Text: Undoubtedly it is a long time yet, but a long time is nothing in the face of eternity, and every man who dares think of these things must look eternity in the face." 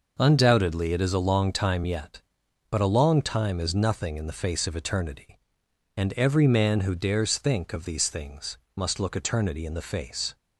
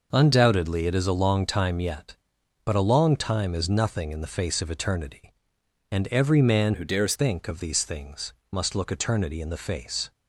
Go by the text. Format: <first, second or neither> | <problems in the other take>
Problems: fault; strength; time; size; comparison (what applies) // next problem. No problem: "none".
first | changes voice from "who" to "dares"; from 6.7 to 7.1 s; 0.4 s long // pauses between "things" and "must"; slight; at 8.3 s; 0.18 s long; slight in the first